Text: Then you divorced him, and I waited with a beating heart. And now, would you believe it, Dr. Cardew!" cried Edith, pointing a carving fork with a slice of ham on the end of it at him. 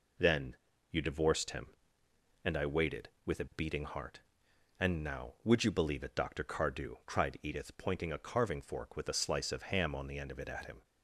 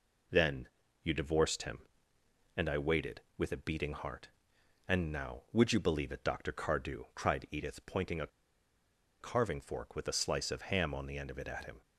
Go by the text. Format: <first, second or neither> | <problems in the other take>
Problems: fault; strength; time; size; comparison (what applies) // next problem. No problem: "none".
first | pauses between "Then" and "you"; slight; at 0.6 s; 0.34 s long; slight in the first // pauses between "a" and "carving"; noticeable; at 8.2 s; 0.93 s long